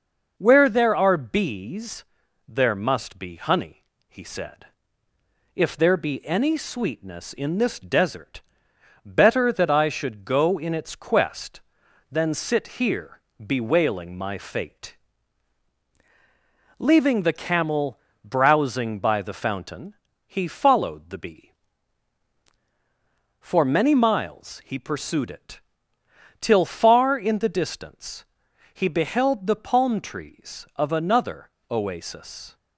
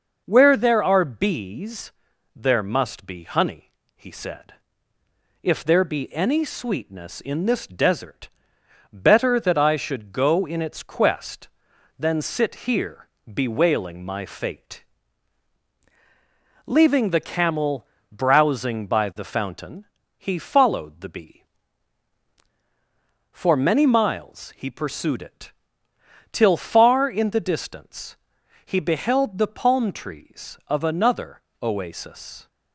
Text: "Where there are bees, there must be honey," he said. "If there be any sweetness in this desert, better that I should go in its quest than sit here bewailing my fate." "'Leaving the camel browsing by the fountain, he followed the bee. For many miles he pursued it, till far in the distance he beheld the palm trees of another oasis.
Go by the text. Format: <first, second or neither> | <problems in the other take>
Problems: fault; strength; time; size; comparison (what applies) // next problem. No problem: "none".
neither | pauses between "here" and "bewailing"; slight; the same in both // pauses between "camel" and "browsing"; slight; the same in both // pauses between "distance" and "he"; noticeable; the same in both // pauses between "another" and "oasis"; slight; the same in both